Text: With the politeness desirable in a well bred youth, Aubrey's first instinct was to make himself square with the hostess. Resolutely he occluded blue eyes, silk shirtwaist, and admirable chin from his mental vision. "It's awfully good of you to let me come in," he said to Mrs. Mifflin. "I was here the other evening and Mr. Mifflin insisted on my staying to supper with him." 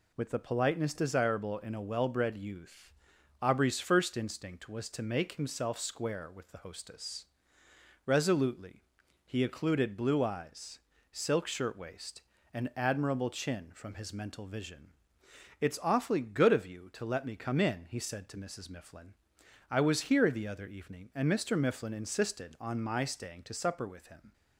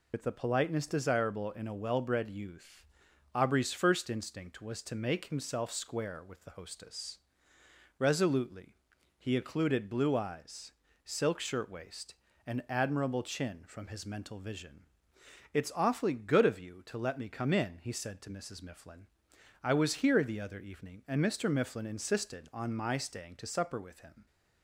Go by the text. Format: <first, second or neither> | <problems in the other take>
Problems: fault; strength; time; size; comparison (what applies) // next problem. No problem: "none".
first | loses the start of "With"; at 0.1 s; 65 ms // pauses between "Resolutely" and "he"; at 8.7 s; 0.44 s long; also in the first